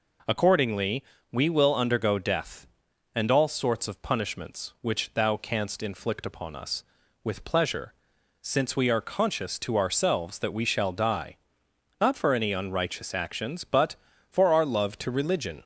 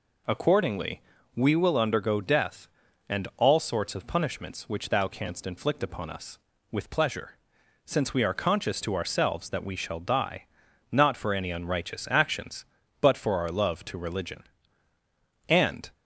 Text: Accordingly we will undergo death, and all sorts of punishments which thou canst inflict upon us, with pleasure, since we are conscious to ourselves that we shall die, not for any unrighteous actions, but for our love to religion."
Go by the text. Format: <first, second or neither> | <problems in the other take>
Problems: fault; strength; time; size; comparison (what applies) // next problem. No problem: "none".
first | pauses between "Accordingly" and "we"; slight; at 1.0 s; 0.32 s long; slight in the first // goes on to say "And"; slight; from 15.4 s on; 0.44 s long